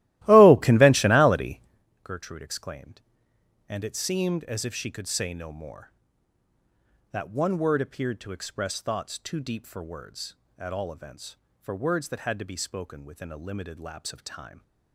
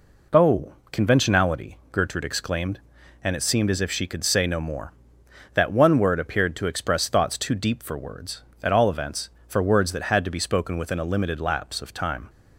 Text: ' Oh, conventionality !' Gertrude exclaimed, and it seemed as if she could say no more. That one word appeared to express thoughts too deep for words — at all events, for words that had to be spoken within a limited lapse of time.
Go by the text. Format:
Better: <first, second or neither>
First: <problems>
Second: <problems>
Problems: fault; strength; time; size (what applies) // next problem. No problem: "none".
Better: second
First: starts louder than the rest; strong; until 1.9 s; 16 dB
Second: none